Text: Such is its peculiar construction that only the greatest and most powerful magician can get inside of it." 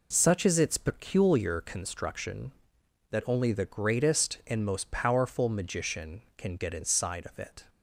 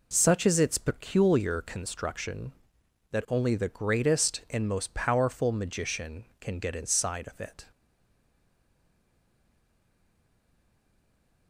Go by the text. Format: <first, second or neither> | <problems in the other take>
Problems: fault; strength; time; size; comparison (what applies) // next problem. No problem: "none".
first | stays silent after the last word; strong; from 7.7 s on; 3.7 s long